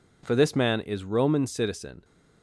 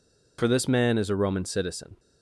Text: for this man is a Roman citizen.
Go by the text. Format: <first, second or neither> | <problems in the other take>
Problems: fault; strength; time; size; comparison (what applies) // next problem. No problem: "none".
second | skips "a"; at 1.0 s